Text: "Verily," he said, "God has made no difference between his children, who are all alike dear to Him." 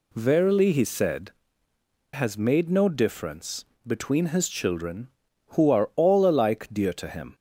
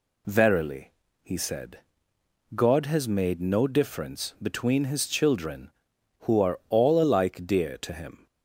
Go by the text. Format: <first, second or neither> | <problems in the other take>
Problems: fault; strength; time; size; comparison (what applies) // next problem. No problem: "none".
second | skips "God"; at 1.7 s // pauses between "difference" and "between"; slight; at 3.6 s; 0.20 s long